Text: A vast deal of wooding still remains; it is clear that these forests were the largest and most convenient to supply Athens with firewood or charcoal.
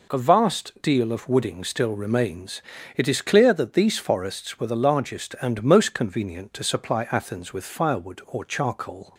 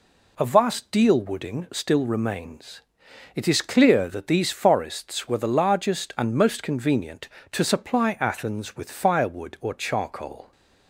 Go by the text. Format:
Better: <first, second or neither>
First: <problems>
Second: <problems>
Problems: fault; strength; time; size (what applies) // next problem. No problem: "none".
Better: first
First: none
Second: skips "of"; at 1.2 s